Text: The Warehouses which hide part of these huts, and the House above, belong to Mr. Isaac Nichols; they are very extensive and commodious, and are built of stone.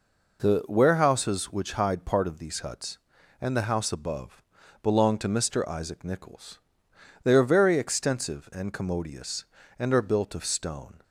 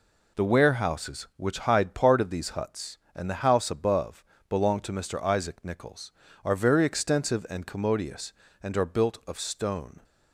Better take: first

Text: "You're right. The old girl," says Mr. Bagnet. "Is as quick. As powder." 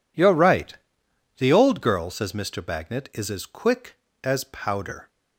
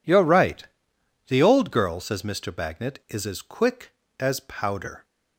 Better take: neither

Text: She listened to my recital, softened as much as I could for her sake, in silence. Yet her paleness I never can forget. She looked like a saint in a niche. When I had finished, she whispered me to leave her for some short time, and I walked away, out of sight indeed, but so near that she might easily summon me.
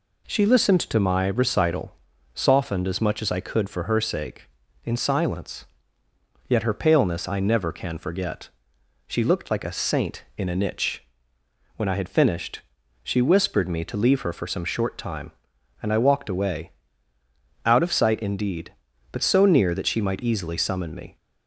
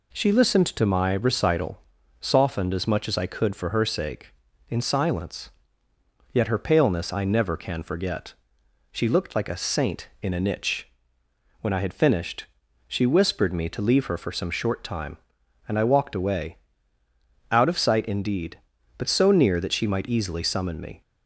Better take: neither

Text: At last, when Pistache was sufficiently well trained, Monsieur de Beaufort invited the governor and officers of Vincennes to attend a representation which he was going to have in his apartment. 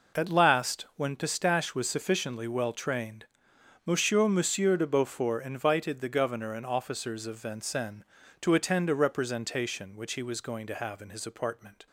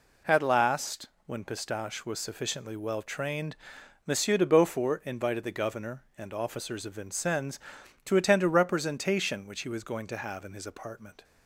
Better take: second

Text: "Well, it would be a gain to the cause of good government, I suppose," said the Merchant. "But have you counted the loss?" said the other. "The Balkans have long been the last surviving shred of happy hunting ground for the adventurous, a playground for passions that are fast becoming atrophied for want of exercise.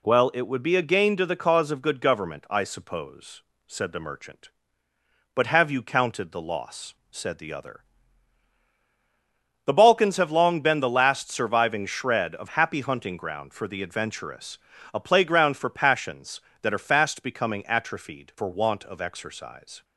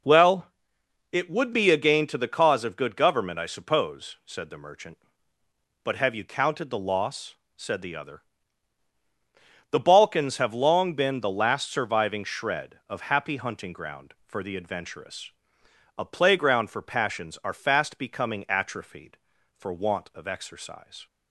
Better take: first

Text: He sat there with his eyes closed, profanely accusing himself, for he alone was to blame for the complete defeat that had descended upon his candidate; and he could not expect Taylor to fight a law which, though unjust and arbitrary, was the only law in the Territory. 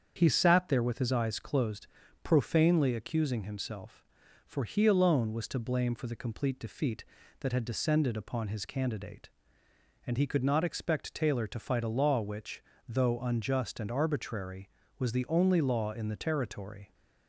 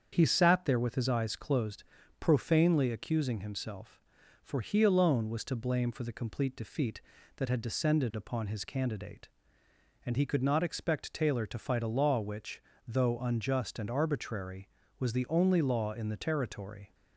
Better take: neither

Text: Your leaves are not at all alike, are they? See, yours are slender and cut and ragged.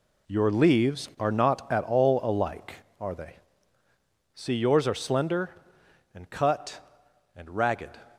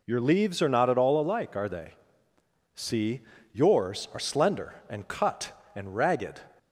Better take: second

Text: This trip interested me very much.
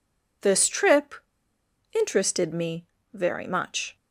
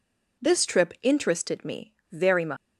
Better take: second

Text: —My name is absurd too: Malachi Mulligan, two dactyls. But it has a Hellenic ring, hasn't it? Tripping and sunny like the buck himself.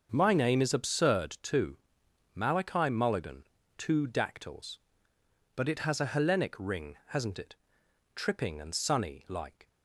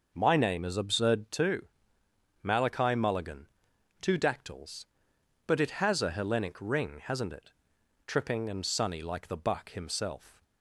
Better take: second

